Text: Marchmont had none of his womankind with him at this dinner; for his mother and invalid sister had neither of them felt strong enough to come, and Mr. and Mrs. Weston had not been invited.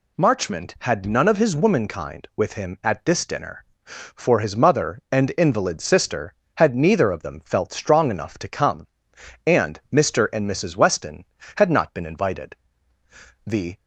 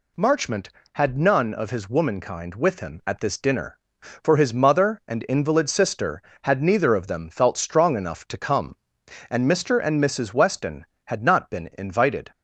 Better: second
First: goes on to say "The"; slight; from 13.4 s on; 0.32 s long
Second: none

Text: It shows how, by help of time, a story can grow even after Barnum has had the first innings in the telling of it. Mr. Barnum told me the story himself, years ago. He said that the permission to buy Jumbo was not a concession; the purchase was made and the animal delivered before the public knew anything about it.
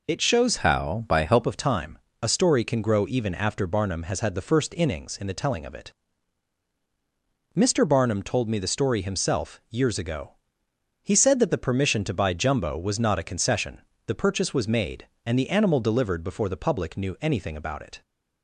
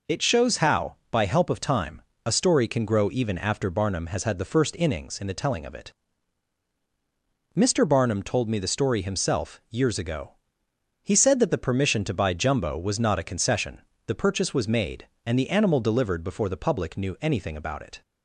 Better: second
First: changes voice from "how" to "help"; from 0.5 to 1.4 s; 0.9 s long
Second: none

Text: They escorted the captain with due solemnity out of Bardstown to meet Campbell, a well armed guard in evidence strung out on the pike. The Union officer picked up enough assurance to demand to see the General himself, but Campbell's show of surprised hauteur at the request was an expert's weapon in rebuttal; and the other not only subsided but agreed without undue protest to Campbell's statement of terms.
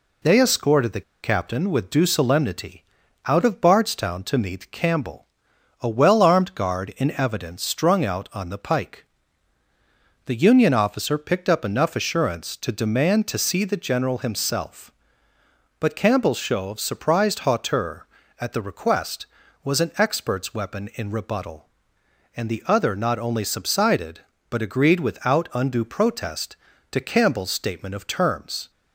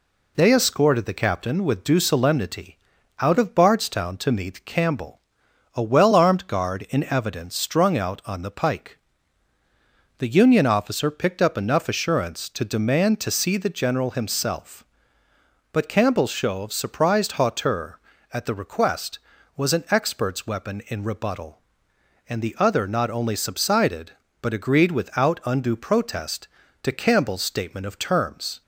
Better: second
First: pauses between "the" and "captain"; slight; at 1.0 s; 0.22 s long // pauses between "solemnity" and "out"; at 2.8 s; 0.44 s long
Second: pauses between "solemnity" and "out"; at 2.7 s; 0.44 s long

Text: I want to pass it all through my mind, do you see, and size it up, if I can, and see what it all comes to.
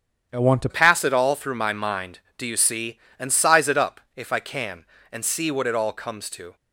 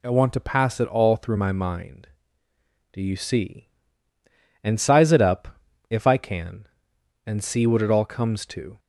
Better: second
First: starts louder than the rest; strong; until 1.3 s; 8.5 dB // changes voice at "pass"; from 0.6 s on; 5.9 s long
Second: none

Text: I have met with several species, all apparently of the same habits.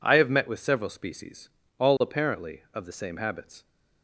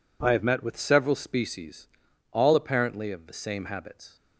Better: neither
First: none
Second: none

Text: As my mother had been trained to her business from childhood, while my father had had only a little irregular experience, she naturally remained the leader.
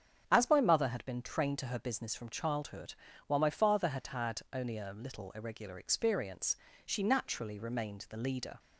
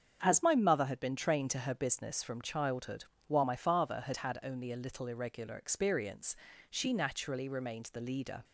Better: neither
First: starts louder than the rest; strong; until 1.3 s; 7.5 dB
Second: starts louder than the rest; strong; until 1.2 s; 7.5 dB

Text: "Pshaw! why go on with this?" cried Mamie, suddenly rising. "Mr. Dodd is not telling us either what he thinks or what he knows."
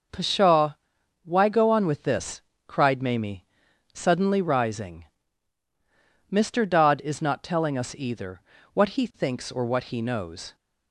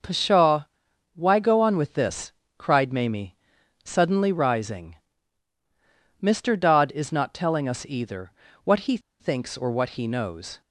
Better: first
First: pauses between "either" and "what"; slight; at 8.3 s; 0.34 s long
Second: pauses between "either" and "what"; slight; at 8.3 s; 0.34 s long // pauses between "he" and "thinks"; slight; at 8.9 s; 0.21 s long

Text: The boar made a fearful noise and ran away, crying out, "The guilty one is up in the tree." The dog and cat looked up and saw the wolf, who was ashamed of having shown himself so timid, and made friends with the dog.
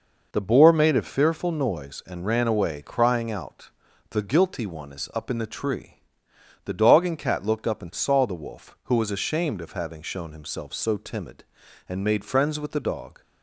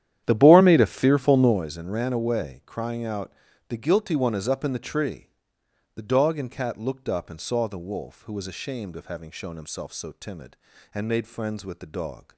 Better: first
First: none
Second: starts louder than the rest; strong; until 1.7 s; 10.5 dB

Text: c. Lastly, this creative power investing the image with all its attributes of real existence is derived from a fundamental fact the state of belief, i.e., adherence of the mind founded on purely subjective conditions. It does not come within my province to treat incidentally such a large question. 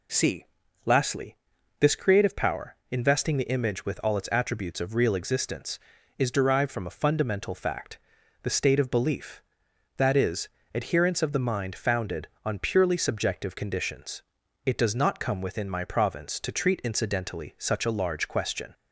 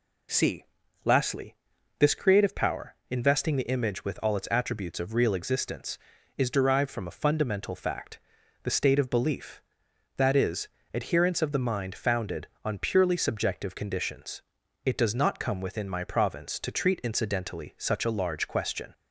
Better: neither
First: pauses between "power" and "investing"; slight; at 2.7 s; 0.16 s long // pauses between "fact" and "the"; at 7.9 s; 0.42 s long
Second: pauses between "power" and "investing"; slight; at 2.9 s; 0.16 s long // pauses between "fact" and "the"; at 8.1 s; 0.42 s long

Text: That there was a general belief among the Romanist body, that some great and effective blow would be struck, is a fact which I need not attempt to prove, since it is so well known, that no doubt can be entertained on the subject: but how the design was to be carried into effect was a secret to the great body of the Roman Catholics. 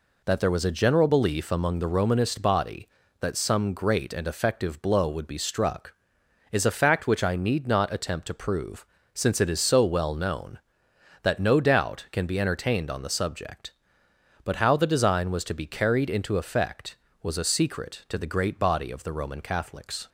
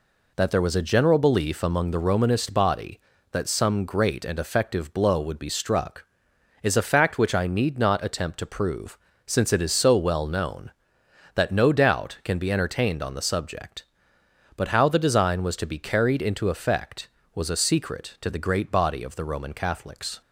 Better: neither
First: none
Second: none

